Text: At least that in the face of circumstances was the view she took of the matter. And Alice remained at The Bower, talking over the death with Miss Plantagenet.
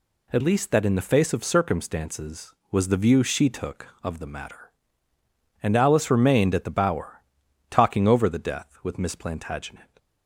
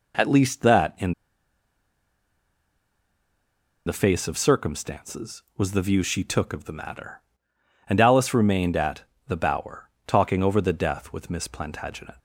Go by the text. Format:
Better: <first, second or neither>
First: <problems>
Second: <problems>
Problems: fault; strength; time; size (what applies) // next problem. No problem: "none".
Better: first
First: none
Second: pauses between "in" and "the"; strong; at 1.1 s; 2.7 s long // pauses between "at" and "The"; slight; at 9.0 s; 0.26 s long